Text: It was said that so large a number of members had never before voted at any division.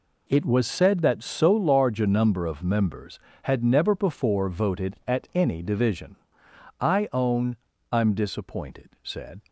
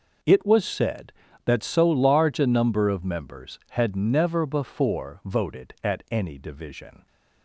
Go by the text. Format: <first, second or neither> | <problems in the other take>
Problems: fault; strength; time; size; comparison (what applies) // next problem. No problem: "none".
second | goes on to say "I own I'm disappointed said"; strong; from 6.8 s on; 2.6 s long